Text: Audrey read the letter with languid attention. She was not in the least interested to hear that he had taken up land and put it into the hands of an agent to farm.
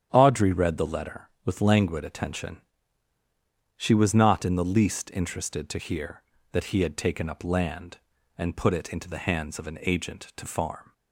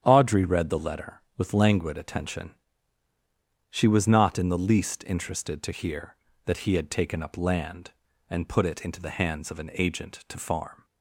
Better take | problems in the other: neither | starts louder than the rest; strong; the same in both

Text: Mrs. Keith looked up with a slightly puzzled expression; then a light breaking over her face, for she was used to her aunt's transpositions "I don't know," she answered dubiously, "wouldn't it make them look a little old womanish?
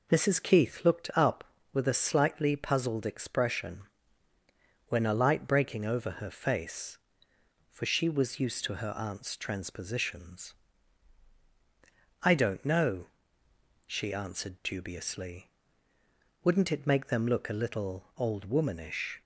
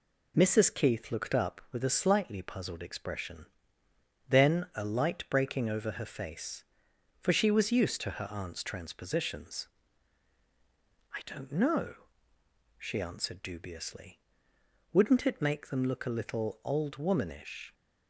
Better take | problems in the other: second | says "when" for "then"; at 4.8 s // pauses between "transpositions" and "I"; strong; at 10.5 s; 1.6 s long; strong in the second

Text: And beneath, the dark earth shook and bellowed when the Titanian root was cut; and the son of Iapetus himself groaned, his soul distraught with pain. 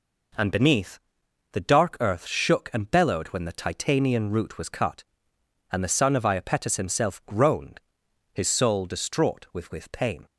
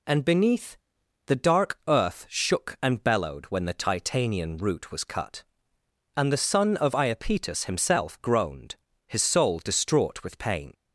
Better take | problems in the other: second | says "with" twice; at 9.6 s

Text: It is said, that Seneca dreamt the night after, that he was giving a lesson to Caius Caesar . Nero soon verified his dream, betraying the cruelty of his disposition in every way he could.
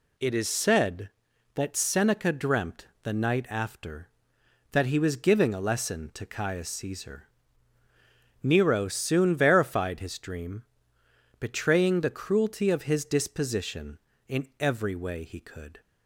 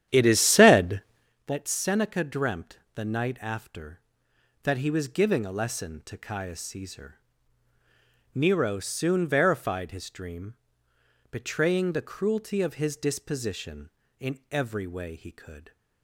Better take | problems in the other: first | starts louder than the rest; strong; until 1.3 s; 10.5 dB // pauses between "dreamt" and "the"; slight; at 2.7 s; 0.16 s long; slight in the first

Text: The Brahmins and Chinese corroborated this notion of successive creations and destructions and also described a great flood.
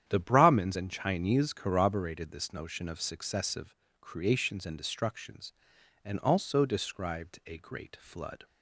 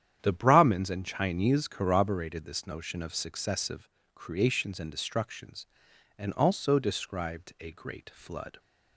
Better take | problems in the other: neither | starts louder than the rest; strong; the same in both // pauses between "successive" and "creations"; slight; the same in both

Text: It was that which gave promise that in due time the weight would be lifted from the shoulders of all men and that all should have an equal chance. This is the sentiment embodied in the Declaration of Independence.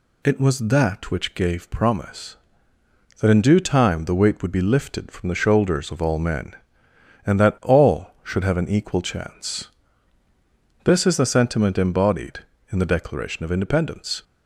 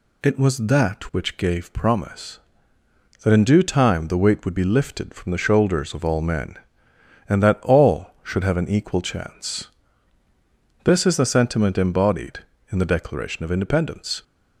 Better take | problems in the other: neither | none

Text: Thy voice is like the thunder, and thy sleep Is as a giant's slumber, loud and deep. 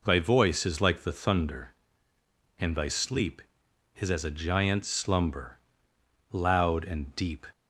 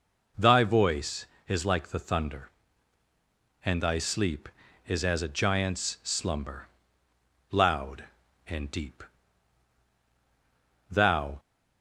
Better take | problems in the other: first | goes on to say "Thou"; slight; from 10.9 s on; 0.48 s long

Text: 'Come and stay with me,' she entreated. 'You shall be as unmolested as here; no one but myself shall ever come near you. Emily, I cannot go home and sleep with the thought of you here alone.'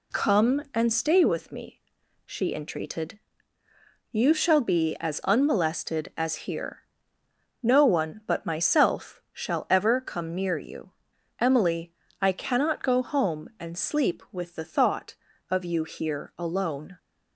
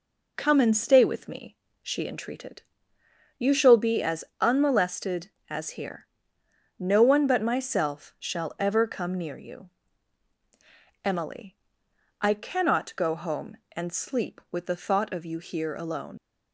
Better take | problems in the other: first | pauses between "as" and "unmolested"; slight; at 4.2 s; 0.16 s long // leaves "alone" unfinished; at 16.1 s; 90 ms

